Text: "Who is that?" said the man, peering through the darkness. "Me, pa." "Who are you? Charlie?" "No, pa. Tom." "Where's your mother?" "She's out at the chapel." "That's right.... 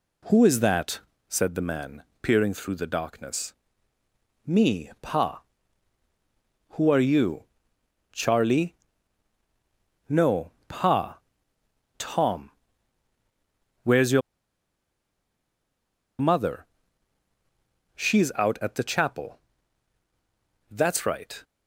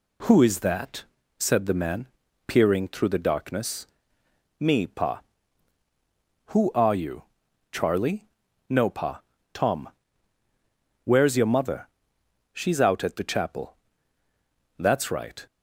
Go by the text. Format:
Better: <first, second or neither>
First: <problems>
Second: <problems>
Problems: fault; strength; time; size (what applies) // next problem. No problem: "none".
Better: second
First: pauses between "your" and "mother"; strong; at 14.2 s; 2.0 s long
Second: none